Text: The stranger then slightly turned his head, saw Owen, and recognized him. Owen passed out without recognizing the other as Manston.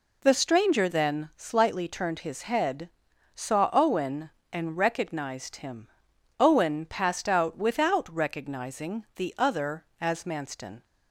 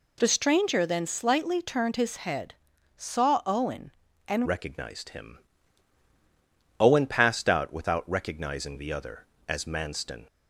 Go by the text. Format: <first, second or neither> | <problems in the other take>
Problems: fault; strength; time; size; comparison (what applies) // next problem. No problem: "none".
first | changes voice at "recognized"; from 4.4 s on; 5.8 s long